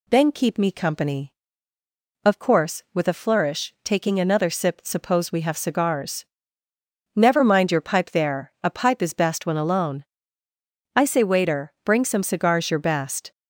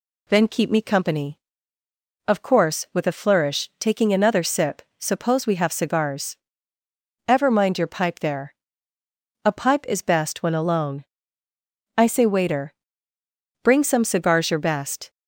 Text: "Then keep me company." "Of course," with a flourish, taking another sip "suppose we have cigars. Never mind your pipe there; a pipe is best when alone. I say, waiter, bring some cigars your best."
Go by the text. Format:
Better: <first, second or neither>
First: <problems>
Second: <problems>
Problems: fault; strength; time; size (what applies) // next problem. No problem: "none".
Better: first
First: none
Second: pauses between "sip" and "suppose"; slight; at 4.8 s; 0.16 s long // says "Ever" for "Never"; at 7.2 s